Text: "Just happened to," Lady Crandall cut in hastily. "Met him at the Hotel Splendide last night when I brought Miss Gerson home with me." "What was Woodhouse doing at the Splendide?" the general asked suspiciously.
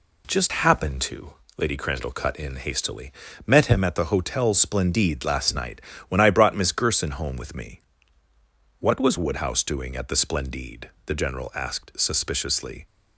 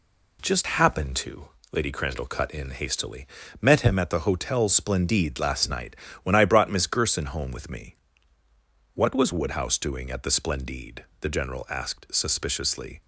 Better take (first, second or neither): neither